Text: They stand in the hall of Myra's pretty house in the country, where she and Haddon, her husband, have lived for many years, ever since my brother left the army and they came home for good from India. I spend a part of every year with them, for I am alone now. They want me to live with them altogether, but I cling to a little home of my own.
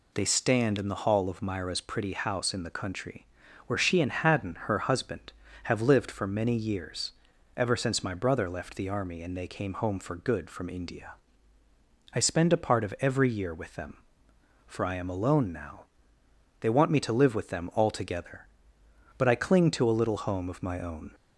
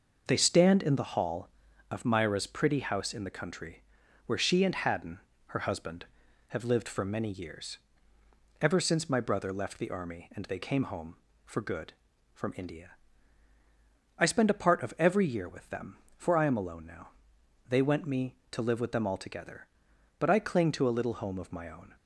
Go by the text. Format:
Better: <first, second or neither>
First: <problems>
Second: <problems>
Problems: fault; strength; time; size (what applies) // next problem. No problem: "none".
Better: first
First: none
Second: says "went" for "want"; at 17.8 s